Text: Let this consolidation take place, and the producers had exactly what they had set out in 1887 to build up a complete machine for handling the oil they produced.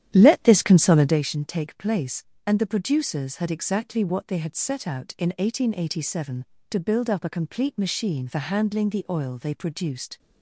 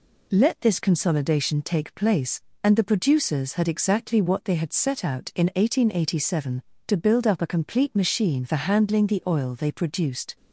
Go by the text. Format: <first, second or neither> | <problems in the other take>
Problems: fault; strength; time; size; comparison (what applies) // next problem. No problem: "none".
second | starts louder than the rest; strong; until 1.2 s; 11 dB